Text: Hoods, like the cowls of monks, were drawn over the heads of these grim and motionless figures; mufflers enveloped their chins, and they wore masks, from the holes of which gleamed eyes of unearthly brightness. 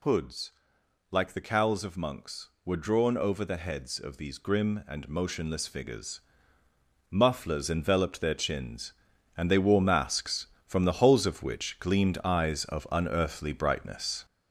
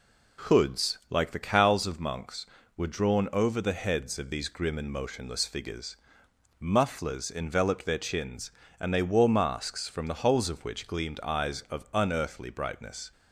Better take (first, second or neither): second